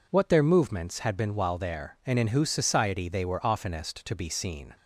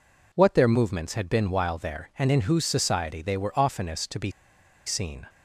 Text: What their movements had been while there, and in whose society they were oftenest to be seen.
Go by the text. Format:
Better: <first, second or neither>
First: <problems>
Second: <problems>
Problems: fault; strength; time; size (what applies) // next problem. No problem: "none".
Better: first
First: none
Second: pauses between "be" and "seen"; noticeable; at 4.3 s; 0.54 s long